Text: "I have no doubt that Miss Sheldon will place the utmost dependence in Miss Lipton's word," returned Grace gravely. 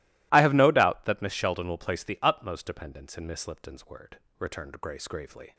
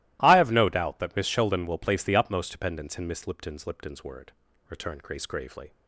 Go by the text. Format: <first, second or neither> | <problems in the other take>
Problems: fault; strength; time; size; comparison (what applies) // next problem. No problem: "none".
first | starts louder than the rest; strong; until 1.2 s; 17.5 dB // says "Lipton's" twice; at 3.6 s